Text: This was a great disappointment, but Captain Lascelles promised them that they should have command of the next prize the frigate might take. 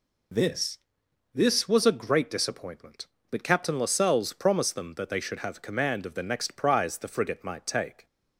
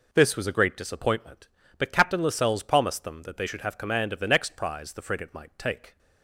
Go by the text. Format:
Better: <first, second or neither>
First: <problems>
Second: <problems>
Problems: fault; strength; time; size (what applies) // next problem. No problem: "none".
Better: second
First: says "This" twice; at 1.3 s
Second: none